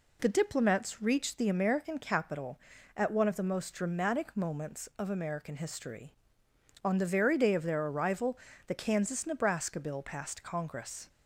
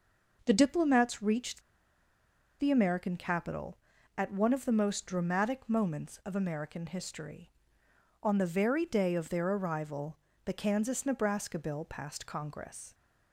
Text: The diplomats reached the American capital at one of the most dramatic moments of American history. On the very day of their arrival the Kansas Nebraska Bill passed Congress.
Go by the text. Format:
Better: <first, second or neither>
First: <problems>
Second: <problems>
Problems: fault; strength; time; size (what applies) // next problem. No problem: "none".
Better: first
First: pauses between "arrival" and "the"; slight; at 8.3 s; 0.30 s long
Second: pauses between "reached" and "the"; at 1.6 s; 0.99 s long // pauses between "arrival" and "the"; slight; at 10.1 s; 0.30 s long